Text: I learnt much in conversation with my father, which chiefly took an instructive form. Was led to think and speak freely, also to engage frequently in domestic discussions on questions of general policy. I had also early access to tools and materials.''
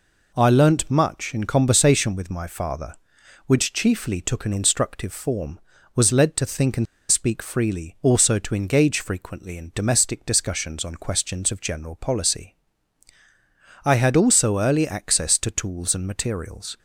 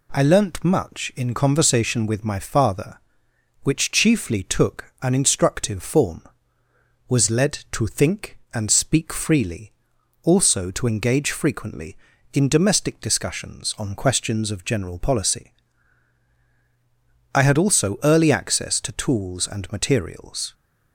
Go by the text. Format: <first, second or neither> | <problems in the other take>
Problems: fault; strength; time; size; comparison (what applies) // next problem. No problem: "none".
second | pauses between "and" and "speak"; slight; at 6.8 s; 0.26 s long